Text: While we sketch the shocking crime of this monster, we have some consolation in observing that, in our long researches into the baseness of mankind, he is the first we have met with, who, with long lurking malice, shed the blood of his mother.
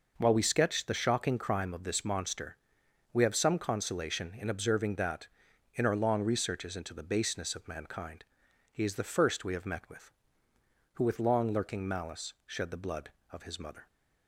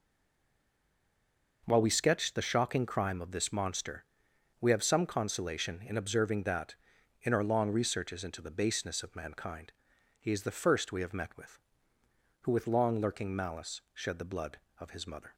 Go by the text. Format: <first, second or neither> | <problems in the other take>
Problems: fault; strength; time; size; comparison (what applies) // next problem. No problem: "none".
first | stays silent before the first word; noticeable; until 1.6 s; 1.6 s long